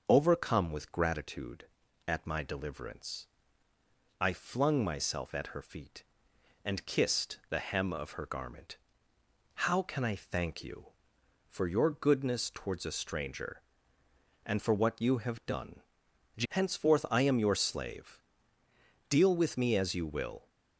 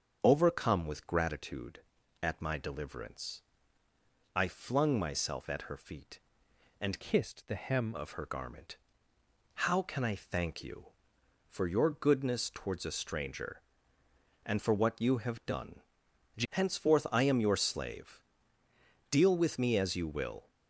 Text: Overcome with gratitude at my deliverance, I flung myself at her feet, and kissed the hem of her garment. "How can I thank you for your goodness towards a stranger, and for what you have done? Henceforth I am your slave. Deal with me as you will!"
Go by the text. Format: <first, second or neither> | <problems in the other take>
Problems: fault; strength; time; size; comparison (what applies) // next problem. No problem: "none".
first | starts louder than the rest; until 1.2 s; 7 dB; also in the first // changes voice from "kissed" to "hem"; from 7.0 to 7.9 s; 0.9 s long